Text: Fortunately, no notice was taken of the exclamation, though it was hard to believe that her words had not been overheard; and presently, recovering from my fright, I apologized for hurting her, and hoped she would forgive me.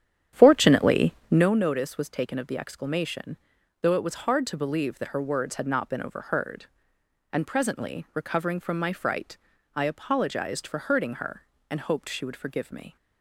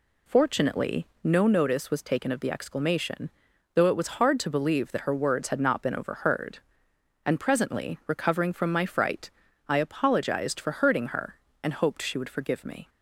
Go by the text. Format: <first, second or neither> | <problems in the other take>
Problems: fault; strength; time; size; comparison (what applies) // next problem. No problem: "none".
second | starts louder than the rest; strong; until 1.5 s; 10 dB